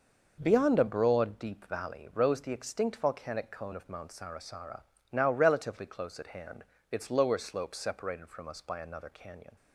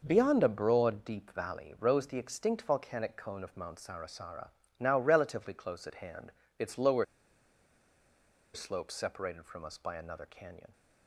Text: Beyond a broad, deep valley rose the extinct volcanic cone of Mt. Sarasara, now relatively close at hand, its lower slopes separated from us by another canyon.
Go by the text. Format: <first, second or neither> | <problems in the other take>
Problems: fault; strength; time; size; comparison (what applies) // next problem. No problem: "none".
first | pauses between "lower" and "slopes"; strong; at 7.0 s; 1.4 s long